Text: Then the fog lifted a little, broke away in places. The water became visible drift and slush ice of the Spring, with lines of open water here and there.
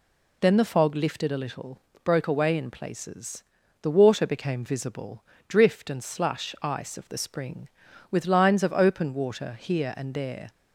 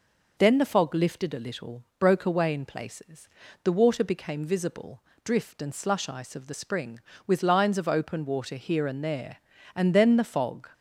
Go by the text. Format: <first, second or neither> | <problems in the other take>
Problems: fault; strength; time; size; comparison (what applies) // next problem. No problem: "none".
first | pauses between "visible" and "drift"; slight; at 5.0 s; 0.22 s long; slight in the first // goes on to say "And then the fog"; noticeable; from 9.7 s on; 0.96 s long